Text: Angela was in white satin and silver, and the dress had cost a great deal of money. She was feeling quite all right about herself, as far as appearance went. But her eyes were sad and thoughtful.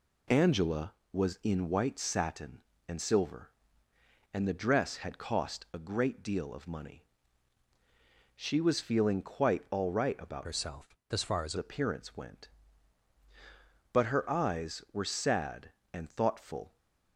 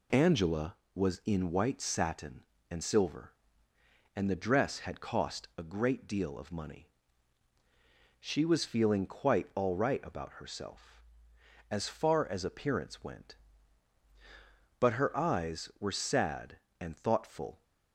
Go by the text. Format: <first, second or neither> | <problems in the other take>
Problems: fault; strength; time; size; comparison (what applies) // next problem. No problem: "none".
second | changes voice from "herself" to "as"; from 10.4 to 11.5 s; 1.1 s long